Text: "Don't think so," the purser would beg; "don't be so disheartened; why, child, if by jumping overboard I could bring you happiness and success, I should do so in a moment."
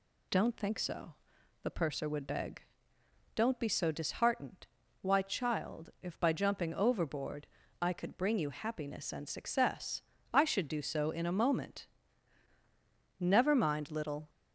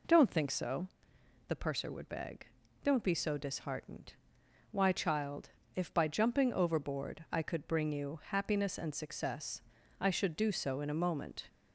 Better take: second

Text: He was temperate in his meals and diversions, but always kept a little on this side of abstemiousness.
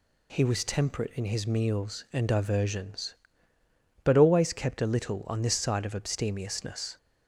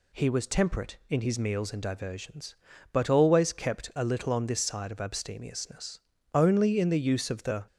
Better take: first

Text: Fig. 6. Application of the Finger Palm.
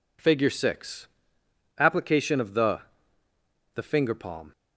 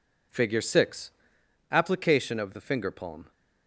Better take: second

